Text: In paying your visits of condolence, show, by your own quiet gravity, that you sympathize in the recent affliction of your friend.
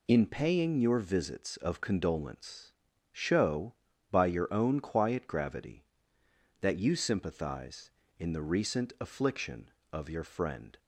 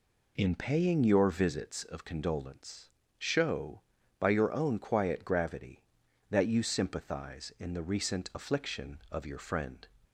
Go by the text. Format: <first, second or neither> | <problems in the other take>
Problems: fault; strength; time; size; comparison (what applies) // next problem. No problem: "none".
neither | none